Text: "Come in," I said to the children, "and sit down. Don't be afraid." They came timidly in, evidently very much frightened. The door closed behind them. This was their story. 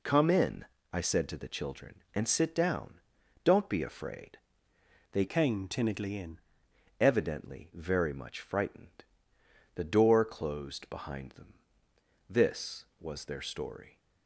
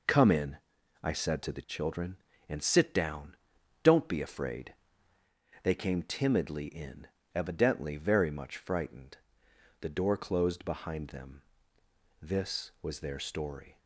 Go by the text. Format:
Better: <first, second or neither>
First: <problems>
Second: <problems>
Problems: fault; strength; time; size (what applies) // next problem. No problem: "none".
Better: second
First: changes voice from "came" to "in"; from 5.2 to 6.3 s; 1.1 s long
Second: none